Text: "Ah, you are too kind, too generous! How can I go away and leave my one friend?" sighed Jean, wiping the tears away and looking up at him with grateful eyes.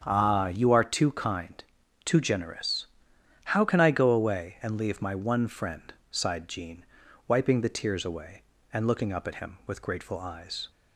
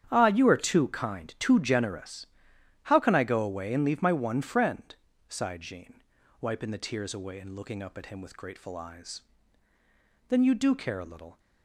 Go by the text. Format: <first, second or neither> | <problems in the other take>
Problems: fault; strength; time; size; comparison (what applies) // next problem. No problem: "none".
first | starts louder than the rest; strong; until 1.1 s; 9 dB; strong in the first // goes on to say "Then you do care a little"; noticeable; from 10.2 s on; 1.1 s long